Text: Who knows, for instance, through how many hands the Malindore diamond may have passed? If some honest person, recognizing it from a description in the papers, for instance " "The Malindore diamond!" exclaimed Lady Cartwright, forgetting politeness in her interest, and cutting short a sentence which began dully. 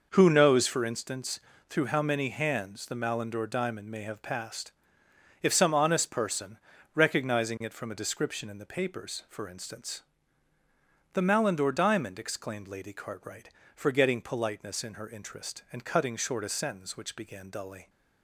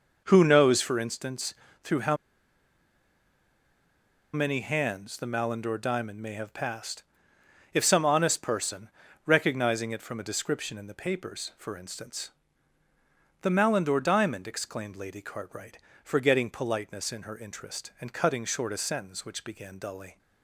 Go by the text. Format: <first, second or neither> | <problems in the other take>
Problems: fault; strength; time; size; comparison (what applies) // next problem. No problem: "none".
first | pauses between "how" and "many"; strong; at 2.1 s; 2.1 s long